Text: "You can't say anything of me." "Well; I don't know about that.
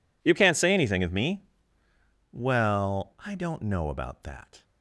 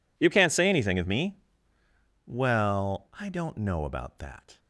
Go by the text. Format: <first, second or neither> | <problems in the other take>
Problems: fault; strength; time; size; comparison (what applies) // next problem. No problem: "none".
neither | none